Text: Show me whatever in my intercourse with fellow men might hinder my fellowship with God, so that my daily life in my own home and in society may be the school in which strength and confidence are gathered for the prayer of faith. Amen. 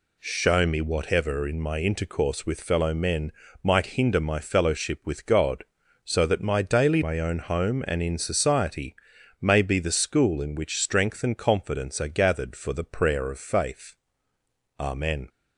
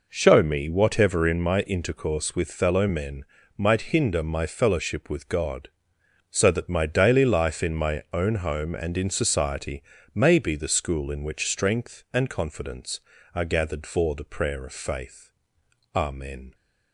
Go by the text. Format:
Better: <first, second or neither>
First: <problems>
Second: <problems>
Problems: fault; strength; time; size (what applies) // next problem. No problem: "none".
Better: second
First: pauses between "men" and "might"; slight; at 3.3 s; 0.32 s long // skips "life in"; at 7.0 s // pauses between "society" and "may"; noticeable; at 8.9 s; 0.46 s long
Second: pauses between "men" and "might"; slight; at 3.2 s; 0.34 s long // pauses between "society" and "may"; slight; at 9.8 s; 0.32 s long